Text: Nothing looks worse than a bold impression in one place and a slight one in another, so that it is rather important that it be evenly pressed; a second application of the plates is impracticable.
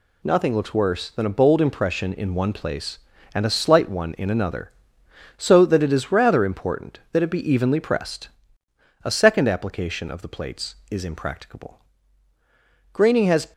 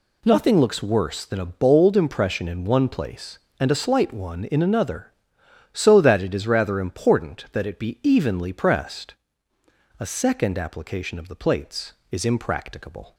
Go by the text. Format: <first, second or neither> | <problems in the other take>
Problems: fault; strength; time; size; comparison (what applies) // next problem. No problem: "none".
second | goes on to say "Graining has"; from 12.9 s on; 0.60 s long